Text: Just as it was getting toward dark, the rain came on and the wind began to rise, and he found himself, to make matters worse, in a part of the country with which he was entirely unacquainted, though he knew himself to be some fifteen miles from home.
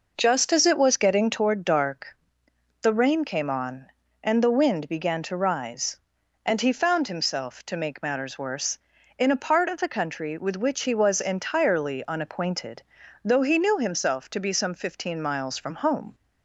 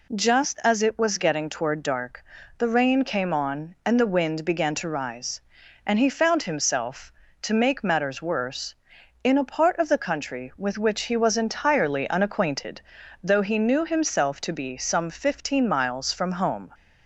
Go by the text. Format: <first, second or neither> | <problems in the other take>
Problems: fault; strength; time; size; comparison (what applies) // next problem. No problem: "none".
neither | none